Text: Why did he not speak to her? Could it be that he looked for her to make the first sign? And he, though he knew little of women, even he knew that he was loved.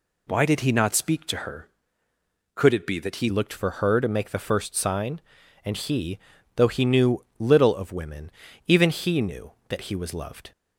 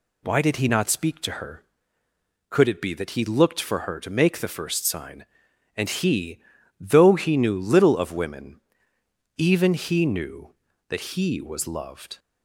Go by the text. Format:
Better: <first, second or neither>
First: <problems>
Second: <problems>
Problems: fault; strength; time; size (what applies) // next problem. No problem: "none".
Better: second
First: changes voice at "looked"; from 3.2 s on; 7.3 s long // pauses between "knew" and "little"; slight; at 7.2 s; 0.16 s long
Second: none